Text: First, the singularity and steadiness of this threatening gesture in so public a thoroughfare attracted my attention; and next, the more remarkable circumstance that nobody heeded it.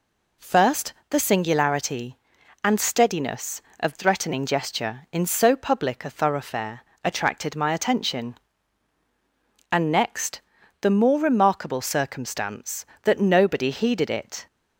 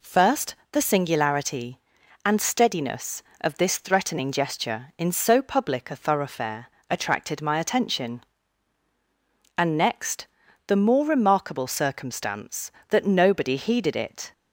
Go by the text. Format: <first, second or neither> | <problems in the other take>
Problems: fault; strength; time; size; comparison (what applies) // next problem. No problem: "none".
second | skips "this"; at 3.9 s // pauses between "thoroughfare" and "attracted"; slight; at 6.8 s; 0.22 s long; slight in the second